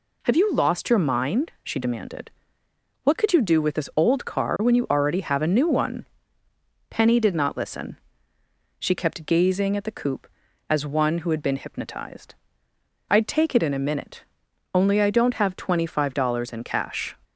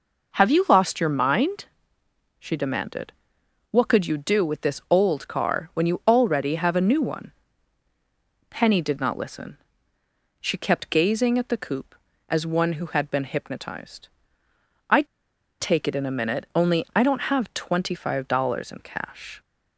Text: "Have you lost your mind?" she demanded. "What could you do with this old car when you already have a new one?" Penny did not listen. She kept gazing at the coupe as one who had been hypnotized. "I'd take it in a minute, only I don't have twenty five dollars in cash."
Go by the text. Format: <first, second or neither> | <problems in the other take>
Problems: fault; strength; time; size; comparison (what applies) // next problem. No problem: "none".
first | pauses between "I'd" and "take"; noticeable; at 15.0 s; 0.53 s long